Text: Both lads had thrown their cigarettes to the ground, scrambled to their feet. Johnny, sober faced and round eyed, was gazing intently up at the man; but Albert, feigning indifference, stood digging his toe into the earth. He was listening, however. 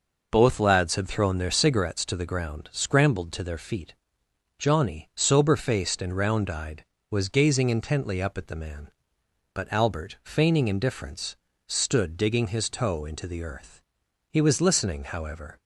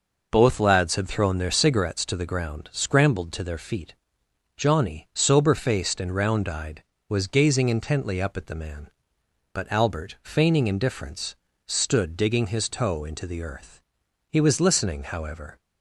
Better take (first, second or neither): neither